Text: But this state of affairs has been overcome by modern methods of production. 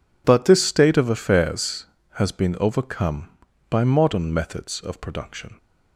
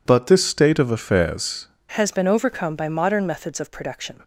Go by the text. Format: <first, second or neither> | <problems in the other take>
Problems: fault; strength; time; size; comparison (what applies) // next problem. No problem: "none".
first | changes voice at "has"; from 1.9 s on; 2.3 s long